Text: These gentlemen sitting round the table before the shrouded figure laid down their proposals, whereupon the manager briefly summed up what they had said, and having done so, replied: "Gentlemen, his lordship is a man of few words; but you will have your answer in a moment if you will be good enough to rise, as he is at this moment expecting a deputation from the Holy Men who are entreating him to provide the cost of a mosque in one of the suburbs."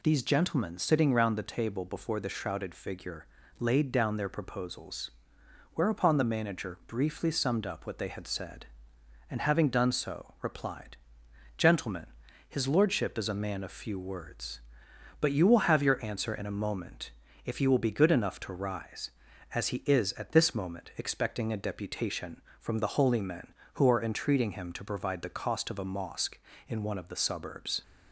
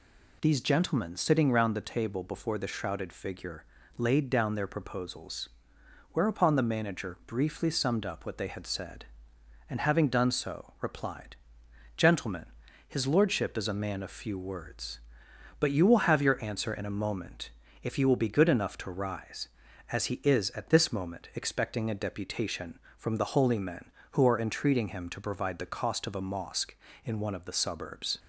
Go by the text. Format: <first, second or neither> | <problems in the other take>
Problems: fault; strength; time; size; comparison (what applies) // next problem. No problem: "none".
neither | pauses between "figure" and "laid"; slight; the same in both // pauses between "moment" and "if"; slight; the same in both